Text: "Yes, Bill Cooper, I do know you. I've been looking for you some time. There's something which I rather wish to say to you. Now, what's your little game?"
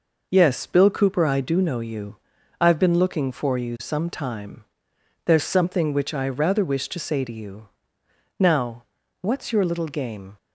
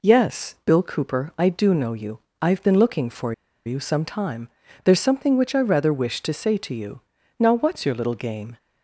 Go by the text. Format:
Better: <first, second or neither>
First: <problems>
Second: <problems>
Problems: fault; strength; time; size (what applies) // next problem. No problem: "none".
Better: first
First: none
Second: pauses between "for" and "you"; slight; at 3.3 s; 0.33 s long